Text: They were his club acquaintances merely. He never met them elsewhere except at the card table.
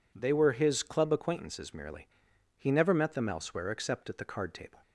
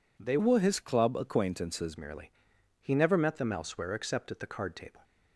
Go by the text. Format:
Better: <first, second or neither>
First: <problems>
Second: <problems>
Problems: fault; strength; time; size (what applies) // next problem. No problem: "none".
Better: first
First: none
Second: changes voice from "were" to "acquaintances"; from 0.3 to 1.9 s; 1.6 s long